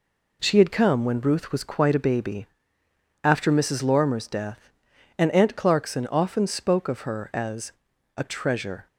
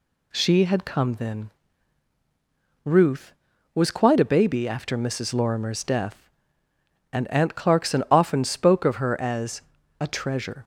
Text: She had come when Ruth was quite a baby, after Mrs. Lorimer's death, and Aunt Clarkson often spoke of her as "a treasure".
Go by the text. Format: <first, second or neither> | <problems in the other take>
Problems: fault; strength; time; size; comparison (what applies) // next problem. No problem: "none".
first | says "then" for "when"; at 1.1 s // pauses between "as" and "a"; at 9.5 s; 0.40 s long; also in the first